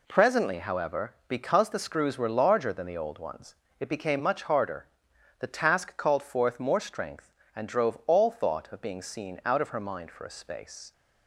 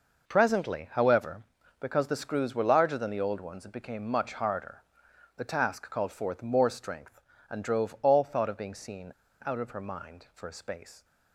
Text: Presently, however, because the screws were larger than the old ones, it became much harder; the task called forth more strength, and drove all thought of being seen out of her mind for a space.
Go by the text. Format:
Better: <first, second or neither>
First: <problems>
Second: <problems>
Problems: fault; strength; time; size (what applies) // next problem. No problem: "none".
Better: first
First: none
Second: pauses between "seen" and "out"; slight; at 9.1 s; 0.34 s long